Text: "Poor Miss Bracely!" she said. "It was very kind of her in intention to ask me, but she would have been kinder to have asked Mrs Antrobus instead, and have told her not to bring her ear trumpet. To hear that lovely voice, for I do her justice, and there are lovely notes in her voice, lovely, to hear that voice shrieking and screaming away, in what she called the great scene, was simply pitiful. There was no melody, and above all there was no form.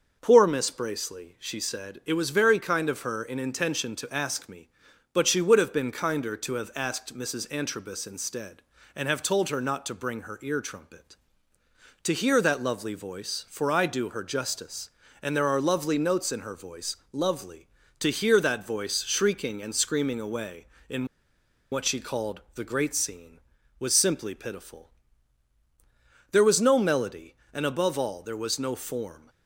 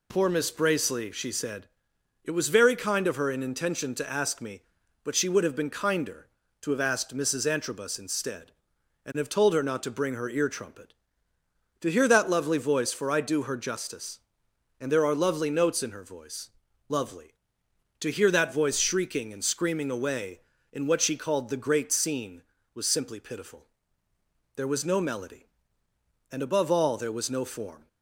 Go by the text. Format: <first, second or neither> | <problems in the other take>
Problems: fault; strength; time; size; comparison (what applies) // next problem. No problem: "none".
second | starts louder than the rest; until 1.2 s; 6.5 dB // pauses between "in" and "what"; noticeable; at 21.0 s; 0.66 s long